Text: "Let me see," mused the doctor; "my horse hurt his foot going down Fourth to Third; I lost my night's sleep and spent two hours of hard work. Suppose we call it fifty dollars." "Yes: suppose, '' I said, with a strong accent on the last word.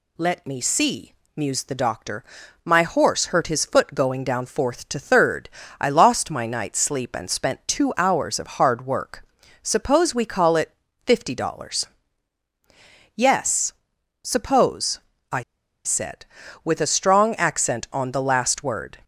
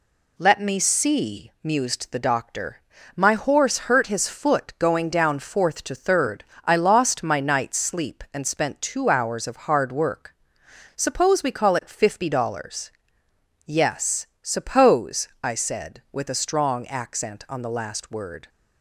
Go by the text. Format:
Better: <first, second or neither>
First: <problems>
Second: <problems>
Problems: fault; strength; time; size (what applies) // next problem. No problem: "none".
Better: second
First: pauses between "it" and "fifty"; slight; at 10.7 s; 0.32 s long // pauses between "I" and "said"; at 15.4 s; 0.43 s long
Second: none